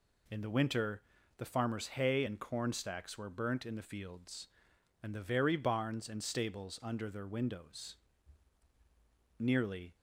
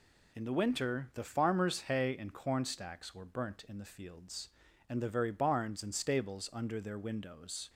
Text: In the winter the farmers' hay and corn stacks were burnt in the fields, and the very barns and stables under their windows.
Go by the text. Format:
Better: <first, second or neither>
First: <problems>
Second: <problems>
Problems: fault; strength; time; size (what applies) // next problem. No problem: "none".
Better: second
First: pauses between "winter" and "the"; slight; at 1.0 s; 0.34 s long // goes on to say "Nearly"; from 9.3 s on; 0.58 s long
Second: none